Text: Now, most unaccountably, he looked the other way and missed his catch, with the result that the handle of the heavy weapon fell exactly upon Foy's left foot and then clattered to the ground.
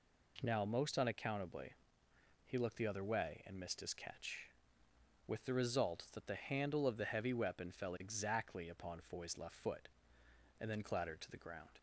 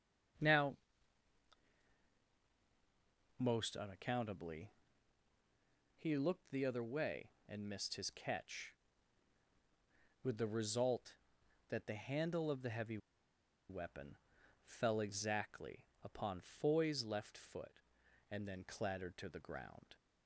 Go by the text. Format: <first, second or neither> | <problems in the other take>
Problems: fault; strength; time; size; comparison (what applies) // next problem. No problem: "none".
first | starts louder than the rest; until 4.0 s; 6.5 dB // pauses between "heavy" and "weapon"; noticeable; at 12.9 s; 0.71 s long // pauses between "weapon" and "fell"; noticeable; at 14.1 s; 0.46 s long // pauses between "exactly" and "upon"; slight; at 15.8 s; 0.18 s long